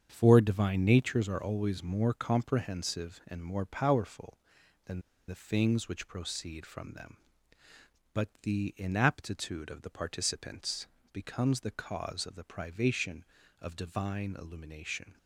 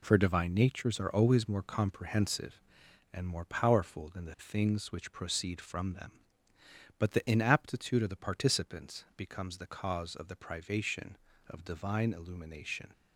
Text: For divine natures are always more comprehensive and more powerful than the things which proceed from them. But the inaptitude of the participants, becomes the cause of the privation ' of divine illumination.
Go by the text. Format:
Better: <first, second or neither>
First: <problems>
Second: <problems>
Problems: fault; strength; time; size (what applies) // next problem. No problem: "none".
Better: second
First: starts louder than the rest; strong; until 1.1 s; 7.5 dB // pauses between "than" and "the"; slight; at 5.0 s; 0.27 s long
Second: none